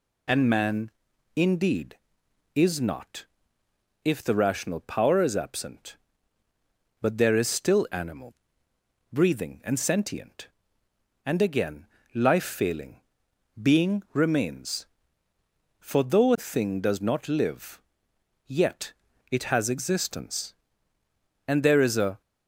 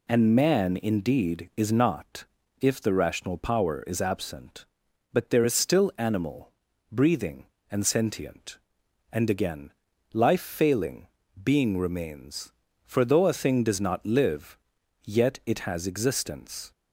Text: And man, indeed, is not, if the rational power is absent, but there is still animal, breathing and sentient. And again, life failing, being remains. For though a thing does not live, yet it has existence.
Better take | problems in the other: second | pauses between "yet" and "it"; at 18.9 s; 0.40 s long // goes on to say "And there is a"; noticeable; from 21.4 s on; 0.72 s long

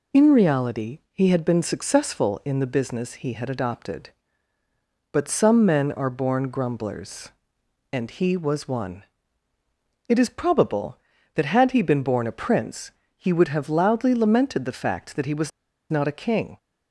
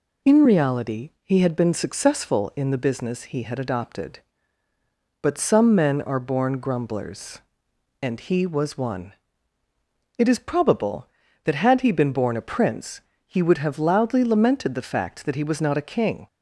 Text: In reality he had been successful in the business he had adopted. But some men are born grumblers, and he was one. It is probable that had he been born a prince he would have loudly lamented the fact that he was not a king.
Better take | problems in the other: second | pauses between "prince" and "he"; slight; at 12.9 s; 0.26 s long; slight in the second // pauses between "was" and "not"; at 15.5 s; 0.40 s long

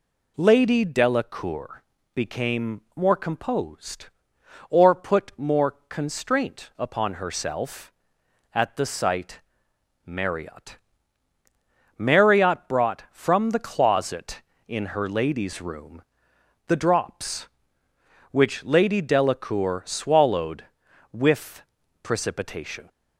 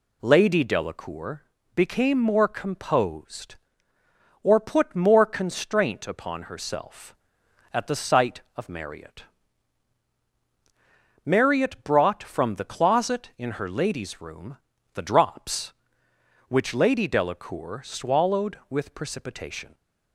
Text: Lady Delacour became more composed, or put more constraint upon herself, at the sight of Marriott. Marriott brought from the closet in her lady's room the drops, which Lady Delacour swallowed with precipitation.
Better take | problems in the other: second | pauses between "Delacour" and "became"; slight; at 1.8 s; 0.32 s long; slight in the second // pauses between "became" and "more"; slight; at 2.8 s; 0.16 s long // skips "of"; at 9.7 s // pauses between "room" and "the"; noticeable; at 16.0 s; 0.64 s long; also in the second // pauses between "with" and "precipitation"; at 21.6 s; 0.40 s long

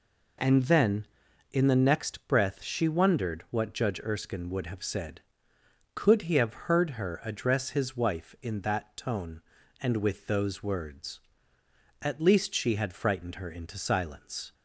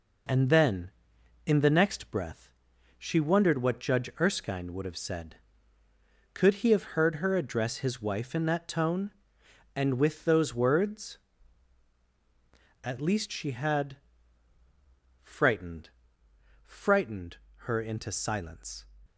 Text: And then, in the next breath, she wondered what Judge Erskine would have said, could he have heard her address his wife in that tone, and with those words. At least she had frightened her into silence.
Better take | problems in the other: first | pauses between "had" and "frightened"; strong; at 13.9 s; 1.2 s long // says "frightened" twice; at 16.6 s

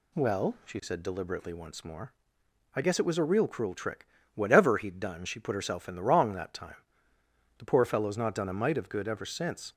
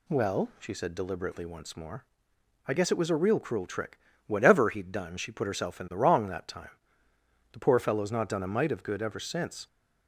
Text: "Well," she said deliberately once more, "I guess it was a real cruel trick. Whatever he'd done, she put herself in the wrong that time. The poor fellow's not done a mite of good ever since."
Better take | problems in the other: neither | none

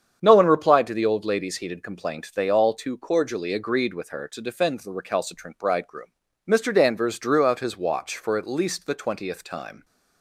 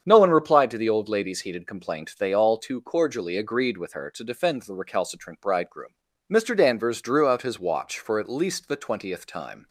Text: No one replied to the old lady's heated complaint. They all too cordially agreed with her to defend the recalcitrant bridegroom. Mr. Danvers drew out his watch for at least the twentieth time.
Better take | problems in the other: neither | starts louder than the rest; strong; the same in both

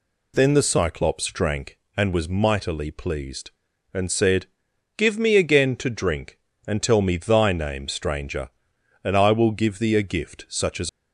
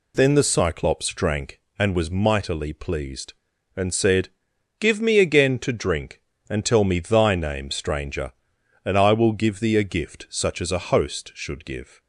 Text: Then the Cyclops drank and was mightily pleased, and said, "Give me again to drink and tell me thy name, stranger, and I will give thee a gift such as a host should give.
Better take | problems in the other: second | stops before "a host should give"; at 10.8 s

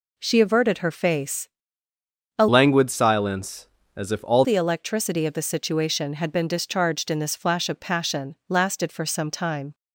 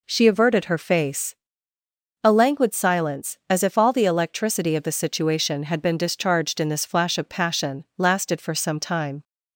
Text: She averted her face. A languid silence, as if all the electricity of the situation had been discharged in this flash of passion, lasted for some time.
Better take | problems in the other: second | changes voice from "languid" to "all"; from 2.4 to 4.4 s; 2.0 s long

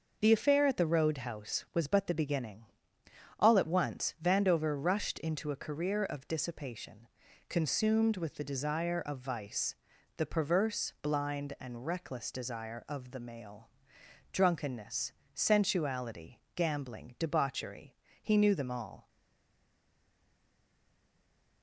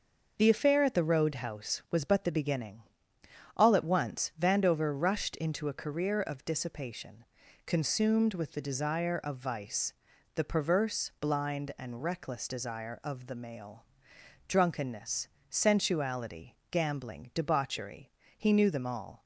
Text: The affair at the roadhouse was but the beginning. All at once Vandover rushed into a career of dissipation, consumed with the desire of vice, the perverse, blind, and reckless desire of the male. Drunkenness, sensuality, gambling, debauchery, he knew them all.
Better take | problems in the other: second | stays silent after the last word; strong; from 19.0 s on; 2.6 s long

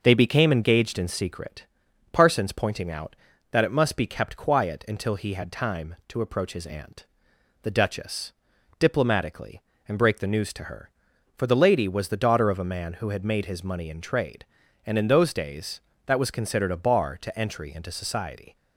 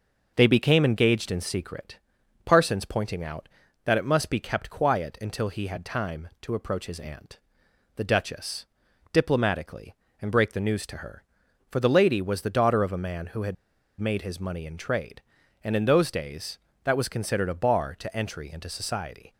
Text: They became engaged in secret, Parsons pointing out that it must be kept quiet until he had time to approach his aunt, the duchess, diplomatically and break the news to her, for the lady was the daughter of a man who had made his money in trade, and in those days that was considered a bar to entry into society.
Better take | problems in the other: first | pauses between "had" and "made"; at 13.5 s; 0.45 s long

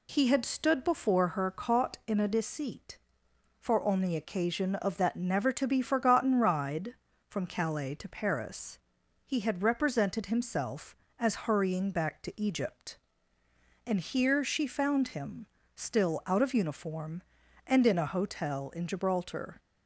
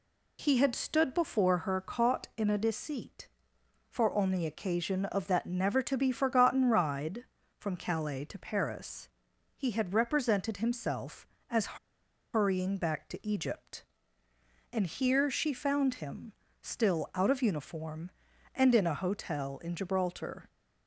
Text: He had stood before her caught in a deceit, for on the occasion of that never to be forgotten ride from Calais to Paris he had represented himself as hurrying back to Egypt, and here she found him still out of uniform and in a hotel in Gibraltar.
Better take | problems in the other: first | pauses between "Paris" and "he"; noticeable; at 9.0 s; 0.48 s long; noticeable in the first // pauses between "as" and "hurrying"; noticeable; at 11.7 s; 0.57 s long // pauses between "him" and "still"; slight; at 16.3 s; 0.30 s long; slight in the first

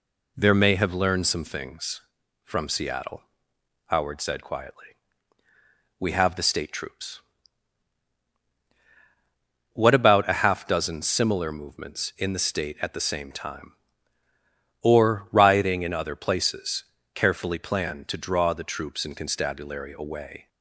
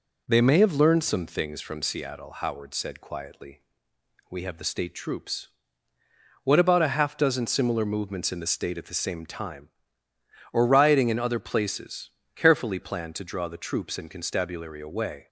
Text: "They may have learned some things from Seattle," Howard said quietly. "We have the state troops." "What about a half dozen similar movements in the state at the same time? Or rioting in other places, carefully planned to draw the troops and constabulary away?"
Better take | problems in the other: second | says "There" for "They"; at 0.3 s

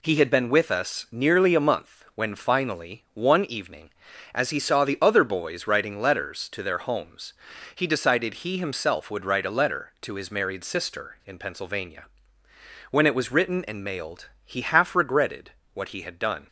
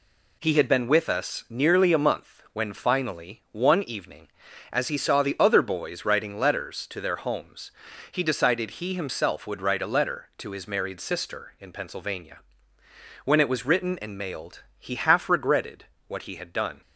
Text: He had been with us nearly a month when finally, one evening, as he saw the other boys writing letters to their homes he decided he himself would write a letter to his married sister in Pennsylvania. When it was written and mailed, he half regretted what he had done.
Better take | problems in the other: neither | pauses between "homes" and "he"; the same in both // pauses between "regretted" and "what"; slight; the same in both

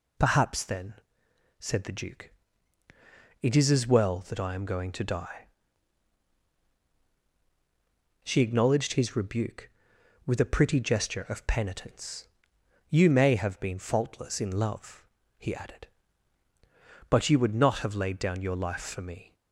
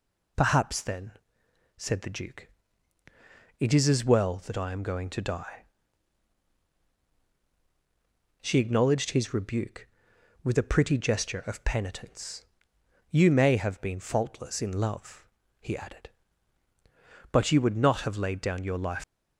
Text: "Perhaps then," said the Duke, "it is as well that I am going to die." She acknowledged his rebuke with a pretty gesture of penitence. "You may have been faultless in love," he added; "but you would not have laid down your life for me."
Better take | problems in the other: first | stops before "for me"; at 19.0 s

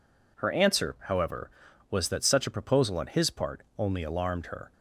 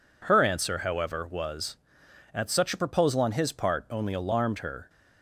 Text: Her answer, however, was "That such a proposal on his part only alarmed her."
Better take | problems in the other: first | says "At" for "That"; at 2.3 s

